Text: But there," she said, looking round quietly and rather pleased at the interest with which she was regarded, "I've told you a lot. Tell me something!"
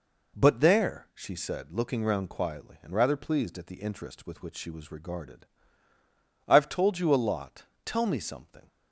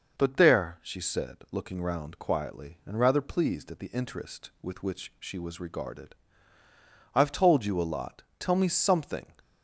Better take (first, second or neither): neither